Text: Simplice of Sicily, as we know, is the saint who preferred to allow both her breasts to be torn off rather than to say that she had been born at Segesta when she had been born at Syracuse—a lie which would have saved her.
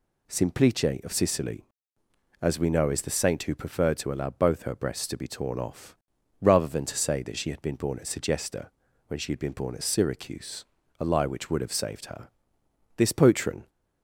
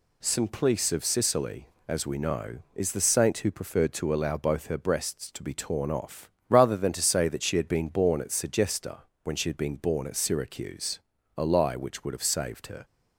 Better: second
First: pauses between "off" and "rather"; noticeable; at 5.9 s; 0.46 s long // pauses between "Segesta" and "when"; at 8.6 s; 0.40 s long // goes on to say "This patron"; noticeable; from 12.9 s on; 0.72 s long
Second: pauses between "off" and "rather"; slight; at 6.2 s; 0.22 s long // pauses between "Segesta" and "when"; slight; at 9.0 s; 0.22 s long

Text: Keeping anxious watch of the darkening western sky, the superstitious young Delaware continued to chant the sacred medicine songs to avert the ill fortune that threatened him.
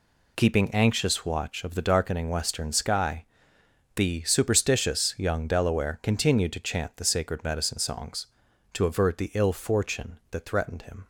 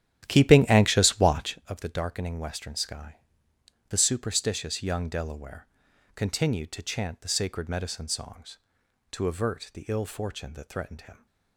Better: first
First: none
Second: starts louder than the rest; strong; until 1.6 s; 12 dB // pauses between "Delaware" and "continued"; noticeable; at 5.6 s; 0.50 s long

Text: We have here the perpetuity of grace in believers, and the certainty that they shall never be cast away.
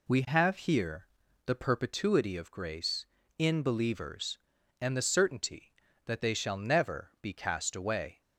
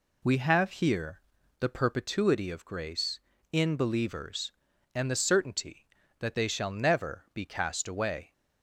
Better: neither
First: pauses between "here" and "the"; at 1.0 s; 0.38 s long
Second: pauses between "here" and "the"; at 1.2 s; 0.38 s long

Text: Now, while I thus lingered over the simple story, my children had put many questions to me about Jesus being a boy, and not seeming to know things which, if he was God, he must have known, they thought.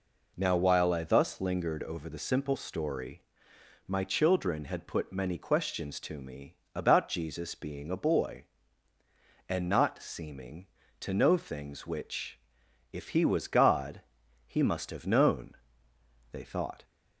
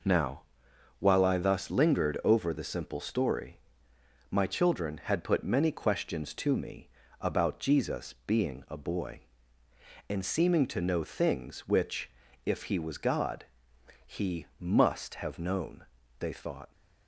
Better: first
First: pauses between "me" and "about"; slight; at 6.5 s; 0.18 s long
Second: pauses between "me" and "about"; slight; at 6.8 s; 0.32 s long // skips "not"; at 10.2 s

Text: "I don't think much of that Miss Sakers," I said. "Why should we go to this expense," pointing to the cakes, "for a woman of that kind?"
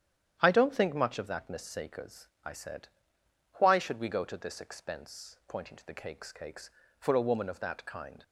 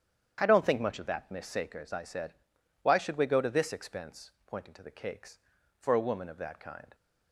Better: second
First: starts louder than the rest; strong; until 1.4 s; 10 dB // says "cakes" twice; at 6.3 s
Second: starts louder than the rest; strong; until 1.4 s; 9 dB

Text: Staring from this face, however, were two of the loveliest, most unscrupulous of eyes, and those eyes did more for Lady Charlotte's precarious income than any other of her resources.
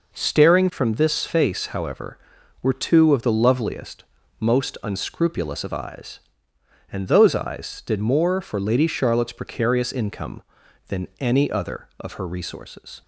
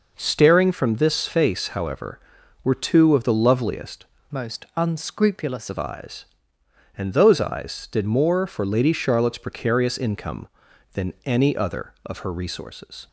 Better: first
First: none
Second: changes voice from "most" to "unscrupulous"; from 4.3 to 5.7 s; 1.4 s long

